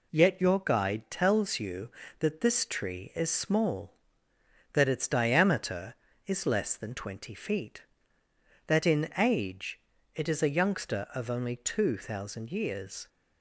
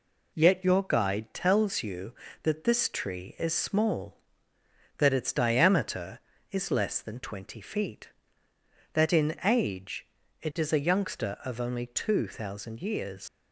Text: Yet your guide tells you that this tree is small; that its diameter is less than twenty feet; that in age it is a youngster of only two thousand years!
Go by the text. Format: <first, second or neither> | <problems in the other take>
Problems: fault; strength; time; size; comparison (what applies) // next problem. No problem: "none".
first | pauses between "age" and "it"; slight; at 10.0 s; 0.34 s long; slight in the first // leaves "years" unfinished; at 13.2 s; 105 ms